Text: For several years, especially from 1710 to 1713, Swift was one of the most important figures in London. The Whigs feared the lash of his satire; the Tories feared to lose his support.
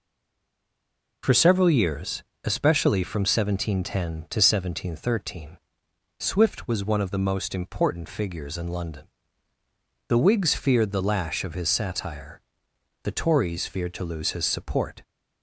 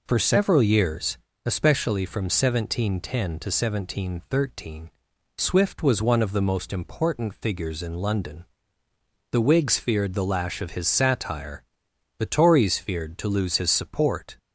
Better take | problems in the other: second | stays silent before the first word; noticeable; until 1.2 s; 1.2 s long

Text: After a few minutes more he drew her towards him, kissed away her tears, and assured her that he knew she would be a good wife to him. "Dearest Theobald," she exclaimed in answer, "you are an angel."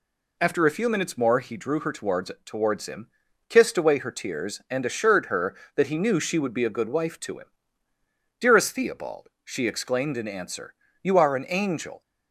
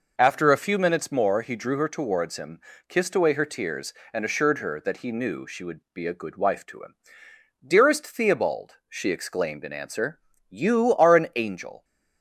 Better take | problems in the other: second | says "towards" twice; at 2.4 s

